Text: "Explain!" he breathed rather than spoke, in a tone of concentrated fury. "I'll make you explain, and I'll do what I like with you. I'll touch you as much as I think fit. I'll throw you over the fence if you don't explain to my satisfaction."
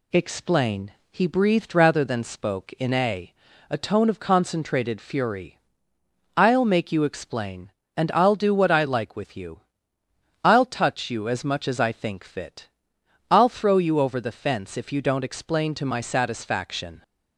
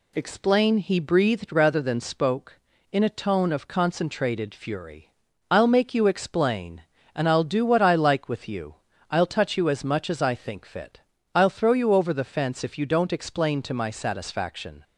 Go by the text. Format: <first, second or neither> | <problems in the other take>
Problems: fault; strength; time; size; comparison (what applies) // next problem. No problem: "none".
second | says "a" twice; at 3.6 s